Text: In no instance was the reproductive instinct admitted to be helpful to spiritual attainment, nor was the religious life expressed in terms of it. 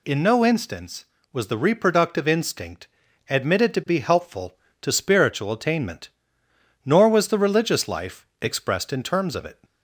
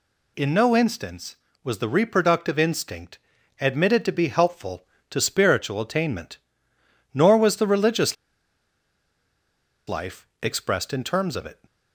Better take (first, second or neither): first